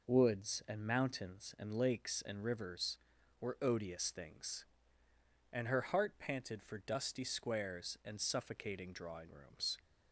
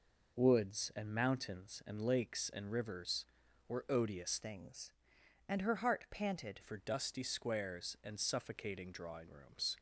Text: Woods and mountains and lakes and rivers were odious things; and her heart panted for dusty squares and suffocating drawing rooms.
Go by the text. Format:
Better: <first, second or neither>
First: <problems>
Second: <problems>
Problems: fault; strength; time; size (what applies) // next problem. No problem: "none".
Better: first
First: none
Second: changes voice from "things" to "panted"; from 4.4 to 6.6 s; 2.2 s long